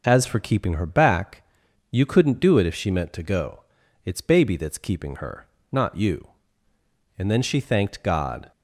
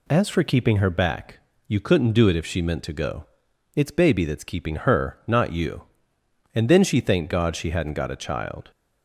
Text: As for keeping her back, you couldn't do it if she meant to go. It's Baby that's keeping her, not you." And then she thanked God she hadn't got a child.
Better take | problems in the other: second | stops before "she hadn't got a child"; at 8.5 s

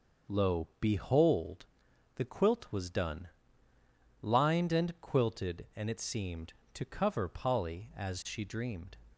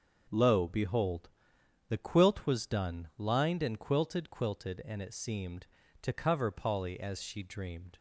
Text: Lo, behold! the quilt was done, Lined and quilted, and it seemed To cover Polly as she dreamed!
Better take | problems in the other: first | starts louder than the rest; until 1.9 s; 6.5 dB; also in the first // says "quilted" twice; at 4.2 s

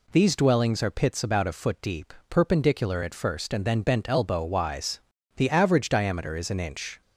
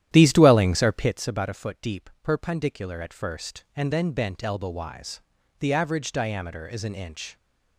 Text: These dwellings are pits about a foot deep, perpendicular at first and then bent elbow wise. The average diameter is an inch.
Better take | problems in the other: first | starts louder than the rest; strong; until 1.3 s; 11.5 dB

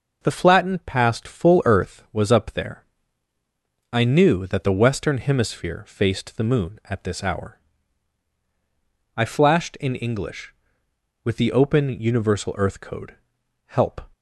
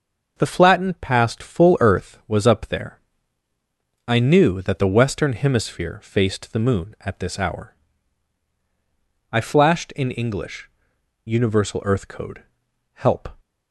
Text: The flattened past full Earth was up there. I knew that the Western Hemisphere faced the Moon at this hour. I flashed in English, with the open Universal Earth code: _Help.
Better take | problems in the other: first | starts louder than the rest; noticeable; until 1.3 s; 6 dB // skips "with the open"; at 10.9 s

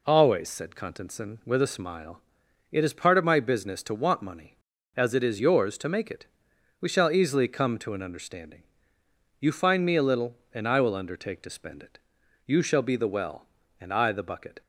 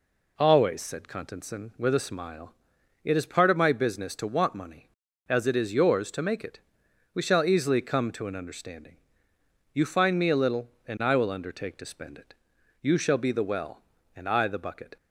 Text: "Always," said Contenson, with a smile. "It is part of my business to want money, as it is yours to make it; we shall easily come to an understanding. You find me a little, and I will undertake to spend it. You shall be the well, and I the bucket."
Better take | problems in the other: neither | none

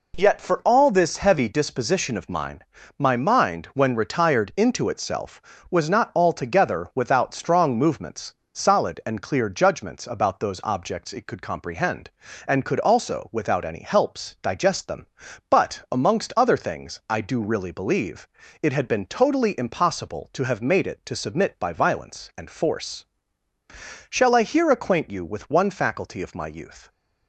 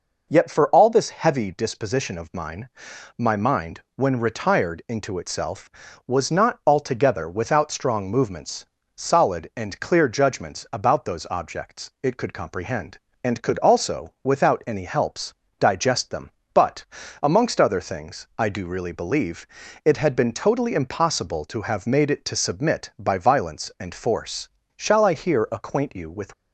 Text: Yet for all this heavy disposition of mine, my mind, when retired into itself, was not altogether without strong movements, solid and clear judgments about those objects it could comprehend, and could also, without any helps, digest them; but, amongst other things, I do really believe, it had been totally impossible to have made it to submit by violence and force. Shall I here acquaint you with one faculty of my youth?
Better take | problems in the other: first | stops before "one faculty of my youth"; at 26.3 s

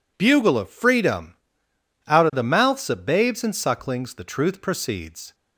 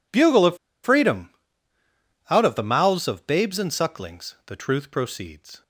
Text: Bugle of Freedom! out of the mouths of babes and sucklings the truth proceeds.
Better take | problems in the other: first | pauses between "of" and "Freedom"; slight; at 0.5 s; 0.27 s long

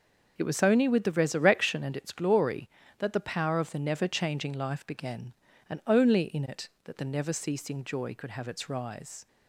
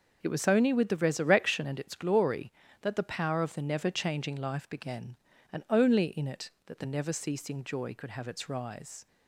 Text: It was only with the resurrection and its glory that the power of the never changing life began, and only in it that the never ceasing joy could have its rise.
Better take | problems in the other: neither | none

